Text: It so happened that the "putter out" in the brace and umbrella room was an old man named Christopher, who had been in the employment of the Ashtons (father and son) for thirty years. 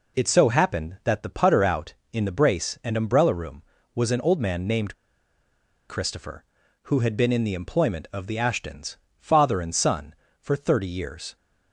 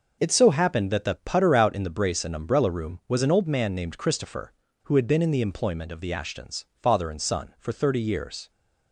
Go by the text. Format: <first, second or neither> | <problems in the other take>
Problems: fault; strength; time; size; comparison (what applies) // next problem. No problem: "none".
second | pauses between "named" and "Christopher"; noticeable; at 4.9 s; 0.94 s long